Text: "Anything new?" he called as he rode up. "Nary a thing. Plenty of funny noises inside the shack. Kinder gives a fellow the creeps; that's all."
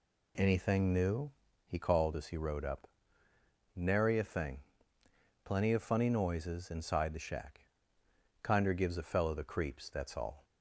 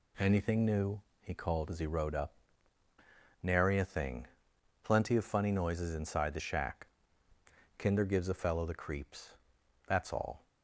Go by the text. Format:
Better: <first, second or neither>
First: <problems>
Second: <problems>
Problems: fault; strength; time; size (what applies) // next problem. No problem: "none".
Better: neither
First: none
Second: none